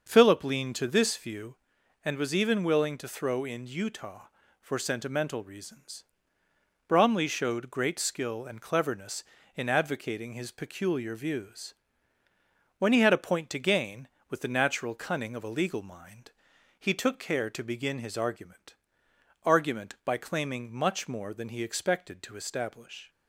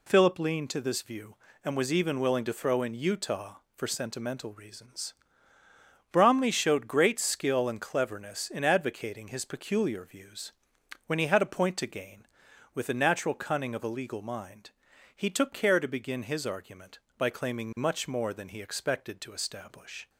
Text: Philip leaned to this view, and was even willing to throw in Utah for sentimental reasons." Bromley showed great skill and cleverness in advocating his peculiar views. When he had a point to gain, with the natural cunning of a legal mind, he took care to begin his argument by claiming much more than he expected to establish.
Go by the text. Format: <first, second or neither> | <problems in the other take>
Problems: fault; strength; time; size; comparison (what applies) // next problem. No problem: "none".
second | starts louder than the rest; until 1.1 s; 6.5 dB // says "argument" twice; at 19.4 s